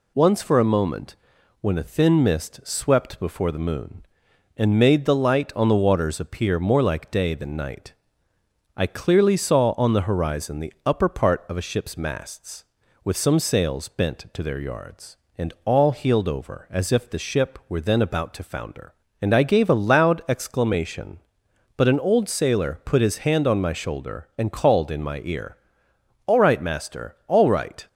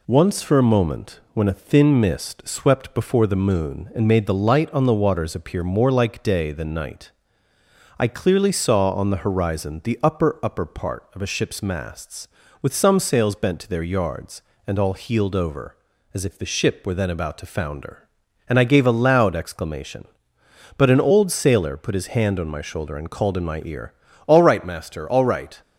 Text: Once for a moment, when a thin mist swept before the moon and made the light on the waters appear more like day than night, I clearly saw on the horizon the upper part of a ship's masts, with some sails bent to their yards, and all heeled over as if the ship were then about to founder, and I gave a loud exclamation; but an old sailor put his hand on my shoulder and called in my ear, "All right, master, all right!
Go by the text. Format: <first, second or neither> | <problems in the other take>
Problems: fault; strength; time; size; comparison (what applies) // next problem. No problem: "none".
first | says "upper" twice; at 10.4 s